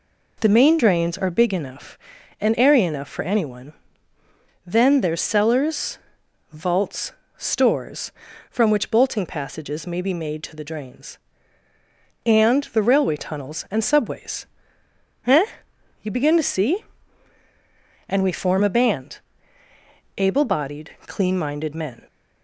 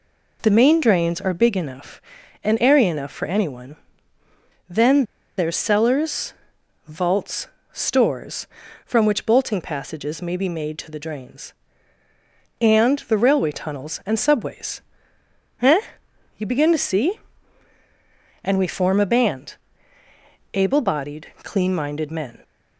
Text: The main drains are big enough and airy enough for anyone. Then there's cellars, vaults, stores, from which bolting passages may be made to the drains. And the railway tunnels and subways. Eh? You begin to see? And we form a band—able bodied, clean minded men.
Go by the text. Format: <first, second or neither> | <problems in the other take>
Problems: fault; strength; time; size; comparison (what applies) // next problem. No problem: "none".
first | pauses between "Then" and "there's"; slight; at 5.0 s; 0.35 s long